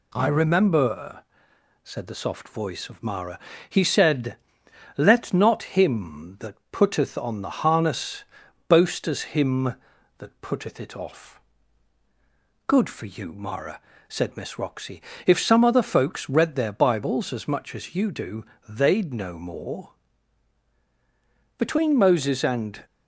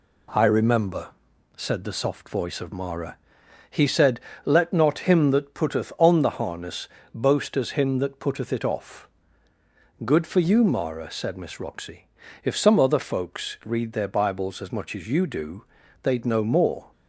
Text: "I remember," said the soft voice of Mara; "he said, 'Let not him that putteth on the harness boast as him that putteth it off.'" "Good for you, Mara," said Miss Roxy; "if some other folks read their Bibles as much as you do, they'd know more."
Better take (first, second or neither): second